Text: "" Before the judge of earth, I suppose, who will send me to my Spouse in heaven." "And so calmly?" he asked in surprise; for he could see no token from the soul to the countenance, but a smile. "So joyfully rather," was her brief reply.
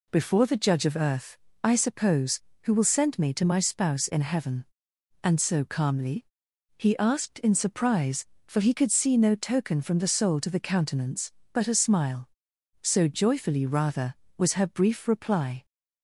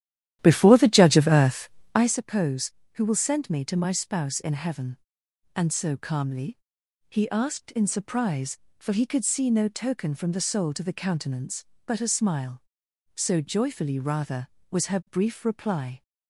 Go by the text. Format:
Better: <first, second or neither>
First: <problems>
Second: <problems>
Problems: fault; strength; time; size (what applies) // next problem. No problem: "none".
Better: first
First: none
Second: starts louder than the rest; strong; until 2.1 s; 12 dB